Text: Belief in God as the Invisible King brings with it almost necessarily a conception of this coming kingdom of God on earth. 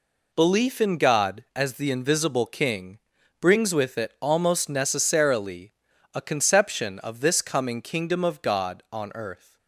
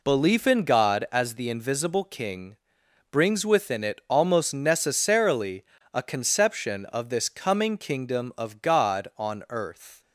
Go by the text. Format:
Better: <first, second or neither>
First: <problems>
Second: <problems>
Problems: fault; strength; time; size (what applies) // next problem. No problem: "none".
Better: first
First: pauses between "King" and "brings"; at 2.9 s; 0.42 s long // pauses between "necessarily" and "a"; at 5.7 s; 0.40 s long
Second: pauses between "King" and "brings"; noticeable; at 2.5 s; 0.56 s long // says "within" for "with"; at 3.4 s // pauses between "necessarily" and "a"; slight; at 5.6 s; 0.30 s long